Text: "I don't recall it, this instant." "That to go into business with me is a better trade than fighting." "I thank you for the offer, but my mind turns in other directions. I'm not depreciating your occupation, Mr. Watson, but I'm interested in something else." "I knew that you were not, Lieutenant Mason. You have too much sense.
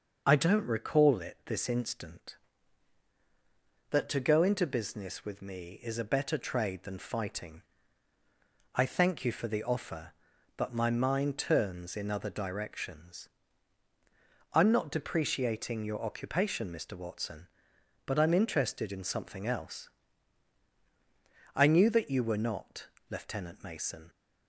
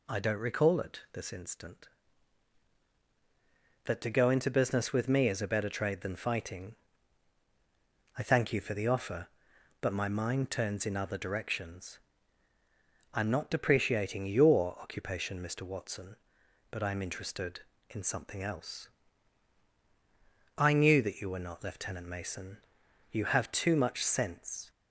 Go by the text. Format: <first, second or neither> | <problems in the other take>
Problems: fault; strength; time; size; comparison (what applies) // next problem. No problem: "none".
second | starts louder than the rest; until 1.2 s; 6.5 dB // stops before "You have too much sense"; at 24.0 s